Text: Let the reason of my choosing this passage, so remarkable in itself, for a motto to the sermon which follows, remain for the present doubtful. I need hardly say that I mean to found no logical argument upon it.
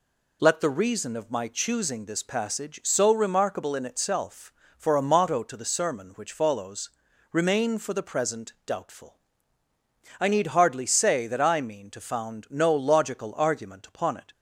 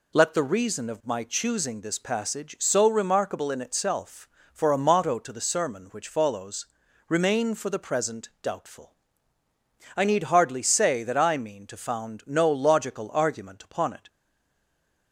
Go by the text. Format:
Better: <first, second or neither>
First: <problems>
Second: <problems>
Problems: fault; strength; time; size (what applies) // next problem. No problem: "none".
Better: first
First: none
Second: stays silent after the last word; from 14.0 s on; 1.1 s long